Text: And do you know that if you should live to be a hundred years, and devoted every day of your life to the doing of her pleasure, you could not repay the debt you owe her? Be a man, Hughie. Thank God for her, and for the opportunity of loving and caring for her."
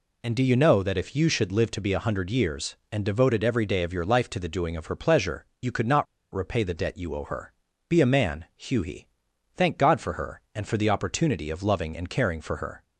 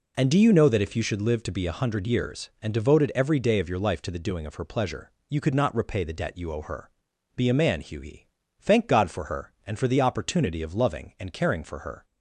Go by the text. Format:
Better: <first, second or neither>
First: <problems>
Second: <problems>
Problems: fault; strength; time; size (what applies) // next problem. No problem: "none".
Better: second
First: pauses between "not" and "repay"; slight; at 6.0 s; 0.29 s long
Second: none